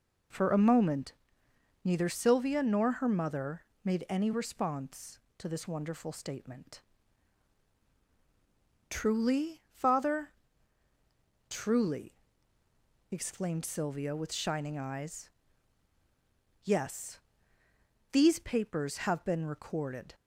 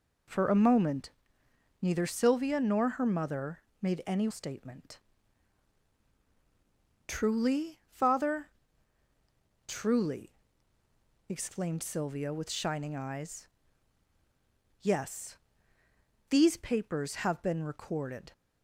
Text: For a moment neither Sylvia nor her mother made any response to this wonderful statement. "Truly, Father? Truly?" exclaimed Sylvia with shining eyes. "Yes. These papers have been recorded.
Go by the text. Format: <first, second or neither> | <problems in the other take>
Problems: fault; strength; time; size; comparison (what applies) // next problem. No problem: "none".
first | pauses between "moment" and "neither"; noticeable; at 1.0 s; 0.72 s long; noticeable in the first // pauses between "mother" and "made"; slight; at 3.6 s; 0.20 s long; slight in the first // skips "response to this wonderful"; at 4.2 s